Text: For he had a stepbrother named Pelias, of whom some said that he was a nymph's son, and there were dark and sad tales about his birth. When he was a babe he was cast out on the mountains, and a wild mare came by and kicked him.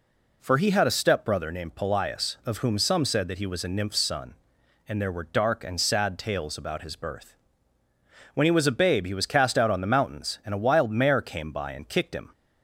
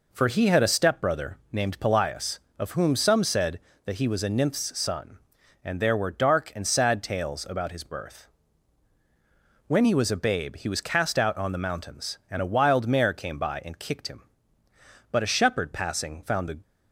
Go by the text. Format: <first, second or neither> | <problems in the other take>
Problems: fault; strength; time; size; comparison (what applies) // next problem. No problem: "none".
first | goes on to say "But a shepherd passing found the"; from 15.1 s on; 1.4 s long